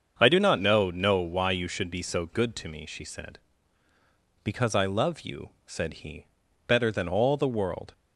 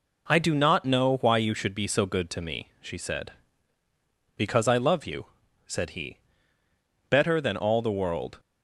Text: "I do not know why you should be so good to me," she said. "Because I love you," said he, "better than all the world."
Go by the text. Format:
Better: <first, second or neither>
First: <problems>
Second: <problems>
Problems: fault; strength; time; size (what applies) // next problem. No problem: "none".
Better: second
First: starts louder than the rest; until 1.2 s; 7 dB // says "know" twice; at 0.9 s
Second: none